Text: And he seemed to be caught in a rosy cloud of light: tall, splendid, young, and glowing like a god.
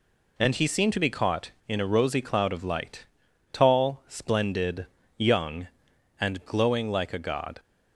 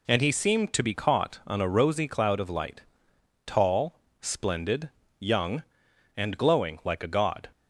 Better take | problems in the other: first | says "on" for "in"; at 1.4 s

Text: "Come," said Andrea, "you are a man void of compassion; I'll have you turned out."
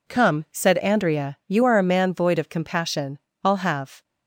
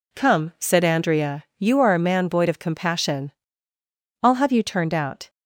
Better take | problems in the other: second | stops before "you turned out"; at 4.0 s

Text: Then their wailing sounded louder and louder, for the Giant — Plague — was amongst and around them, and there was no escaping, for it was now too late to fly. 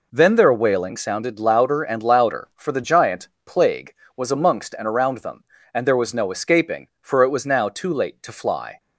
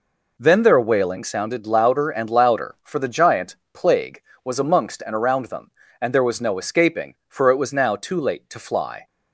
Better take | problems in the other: neither | none

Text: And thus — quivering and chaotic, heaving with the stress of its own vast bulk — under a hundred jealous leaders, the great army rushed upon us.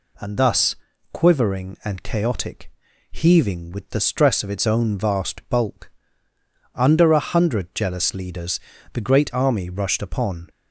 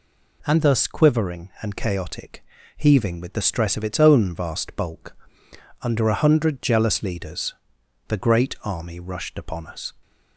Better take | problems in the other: second | stops before "us"; at 10.4 s

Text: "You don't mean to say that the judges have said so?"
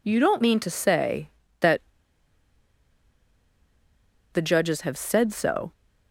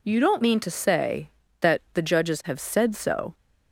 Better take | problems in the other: second | pauses between "that" and "the"; strong; at 1.7 s; 2.5 s long

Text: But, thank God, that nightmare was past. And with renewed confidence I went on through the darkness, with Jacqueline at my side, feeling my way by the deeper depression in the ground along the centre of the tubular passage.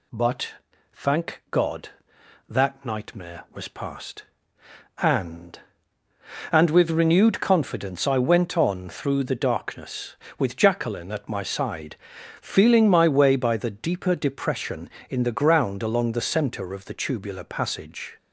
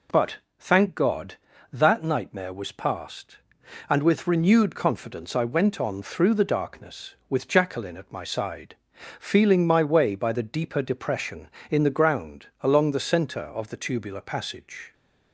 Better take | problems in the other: second | says "And" twice; at 6.4 s

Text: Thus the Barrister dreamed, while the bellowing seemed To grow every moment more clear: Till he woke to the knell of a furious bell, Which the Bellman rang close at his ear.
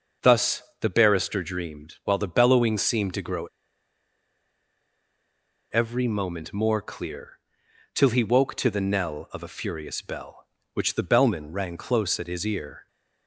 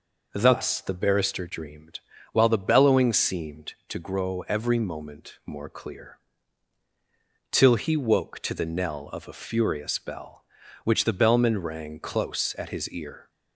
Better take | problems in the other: second | starts louder than the rest; noticeable; until 1.4 s; 6 dB // pauses between "Thus" and "the"; slight; at 0.6 s; 0.18 s long // pauses between "grow" and "every"; strong; at 3.4 s; 2.2 s long

